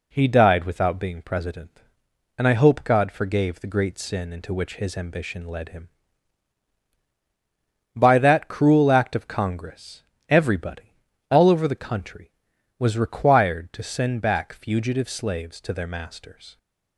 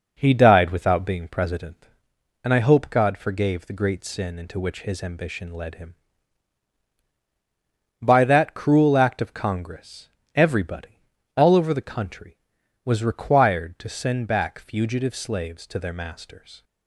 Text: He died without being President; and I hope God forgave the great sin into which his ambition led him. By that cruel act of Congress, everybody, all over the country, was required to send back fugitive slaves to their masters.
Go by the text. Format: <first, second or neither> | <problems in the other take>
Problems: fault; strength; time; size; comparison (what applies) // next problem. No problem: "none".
first | starts louder than the rest; noticeable; until 2.0 s; 5 dB